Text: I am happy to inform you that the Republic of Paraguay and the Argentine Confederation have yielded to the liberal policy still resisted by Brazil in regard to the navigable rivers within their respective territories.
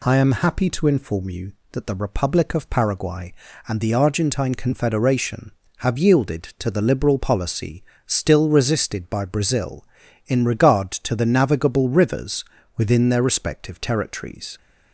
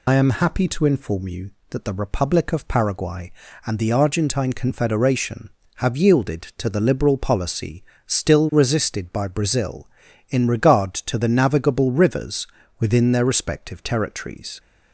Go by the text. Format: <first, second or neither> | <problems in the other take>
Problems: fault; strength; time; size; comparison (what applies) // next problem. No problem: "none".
first | loses the start of "I"; at 0.0 s; 75 ms // pauses between "policy" and "still"; slight; at 7.8 s; 0.24 s long; slight in the first // pauses between "rivers" and "within"; slight; at 12.4 s; 0.34 s long; slight in the first